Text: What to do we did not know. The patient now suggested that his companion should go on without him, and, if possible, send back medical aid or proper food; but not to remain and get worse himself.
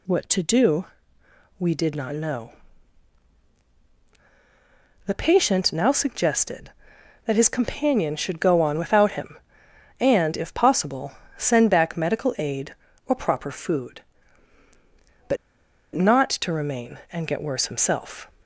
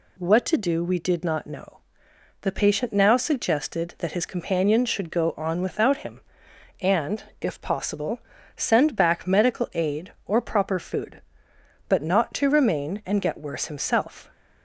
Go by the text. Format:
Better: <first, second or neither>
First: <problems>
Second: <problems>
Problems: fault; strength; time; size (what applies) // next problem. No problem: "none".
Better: second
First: pauses between "do" and "we"; noticeable; at 0.8 s; 0.72 s long // pauses between "but" and "not"; noticeable; at 15.3 s; 0.58 s long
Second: none